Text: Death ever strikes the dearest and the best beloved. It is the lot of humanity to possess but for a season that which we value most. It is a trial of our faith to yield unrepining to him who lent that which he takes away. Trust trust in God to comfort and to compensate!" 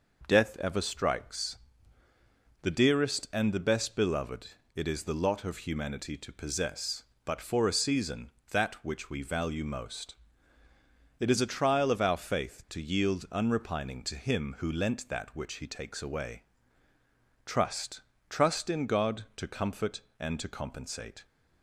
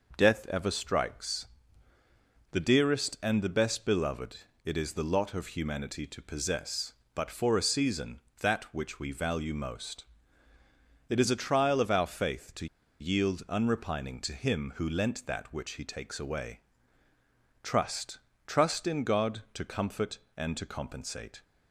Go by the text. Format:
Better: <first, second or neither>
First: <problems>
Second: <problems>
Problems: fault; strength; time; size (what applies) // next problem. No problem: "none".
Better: first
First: pauses between "strikes" and "the"; at 1.5 s; 1.0 s long // pauses between "Trust" and "trust"; slight; at 18.0 s; 0.28 s long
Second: pauses between "strikes" and "the"; at 1.4 s; 1.0 s long // pauses between "to" and "yield"; slight; at 12.6 s; 0.34 s long // pauses between "Trust" and "trust"; slight; at 18.1 s; 0.28 s long